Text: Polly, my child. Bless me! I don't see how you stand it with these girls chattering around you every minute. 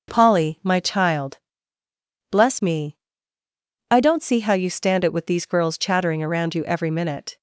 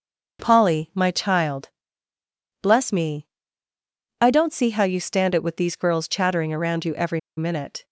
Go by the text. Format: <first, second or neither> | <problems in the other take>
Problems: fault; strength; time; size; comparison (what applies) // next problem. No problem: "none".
first | starts louder than the rest; until 1.4 s; 6.5 dB; also in the first // pauses between "every" and "minute"; slight; at 7.1 s; 0.18 s long